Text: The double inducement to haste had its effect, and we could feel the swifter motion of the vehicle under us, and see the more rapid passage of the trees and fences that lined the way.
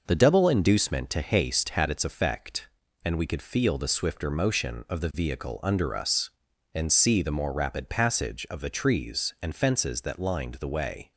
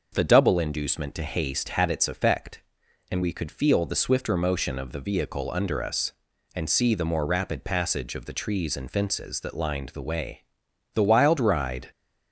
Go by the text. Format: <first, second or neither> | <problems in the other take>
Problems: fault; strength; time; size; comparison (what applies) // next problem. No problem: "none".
first | goes on to say "The wild ride"; noticeable; from 10.9 s on; 0.96 s long